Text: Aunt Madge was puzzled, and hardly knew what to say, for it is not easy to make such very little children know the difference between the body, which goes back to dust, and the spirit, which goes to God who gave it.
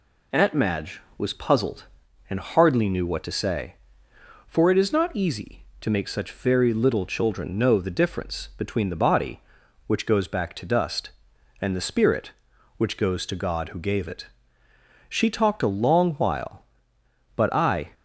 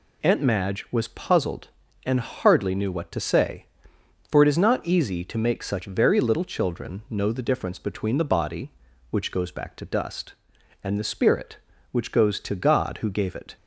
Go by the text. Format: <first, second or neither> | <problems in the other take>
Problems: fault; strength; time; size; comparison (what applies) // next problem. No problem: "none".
second | goes on to say "She talked a long while but I"; strong; from 15.0 s on; 2.8 s long